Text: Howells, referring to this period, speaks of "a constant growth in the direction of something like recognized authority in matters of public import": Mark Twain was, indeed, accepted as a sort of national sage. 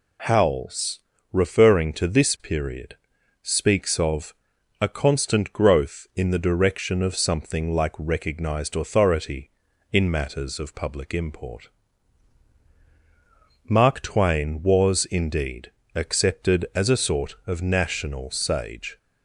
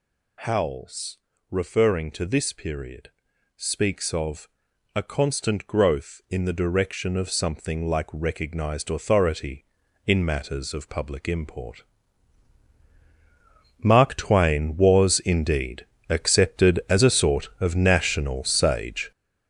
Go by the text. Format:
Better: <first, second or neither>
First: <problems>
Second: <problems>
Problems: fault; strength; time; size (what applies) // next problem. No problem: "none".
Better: first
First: pauses between "of" and "a"; noticeable; at 4.3 s; 0.46 s long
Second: gets louder; strong; throughout; 7.5 dB // pauses between "of" and "a"; noticeable; at 4.4 s; 0.46 s long